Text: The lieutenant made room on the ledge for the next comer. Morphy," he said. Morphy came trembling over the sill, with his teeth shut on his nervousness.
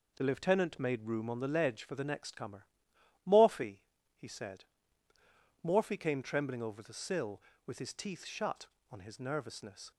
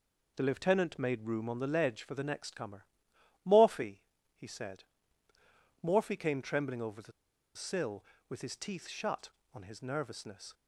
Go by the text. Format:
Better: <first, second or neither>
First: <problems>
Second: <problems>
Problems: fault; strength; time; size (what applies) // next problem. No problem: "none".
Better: first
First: none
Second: pauses between "the" and "sill"; at 7.1 s; 0.43 s long